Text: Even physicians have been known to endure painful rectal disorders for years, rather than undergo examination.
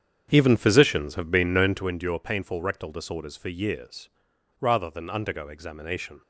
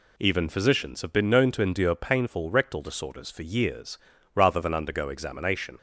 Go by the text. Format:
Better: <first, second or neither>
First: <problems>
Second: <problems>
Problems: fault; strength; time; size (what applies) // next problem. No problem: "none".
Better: second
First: starts louder than the rest; strong; until 1.9 s; 8 dB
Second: none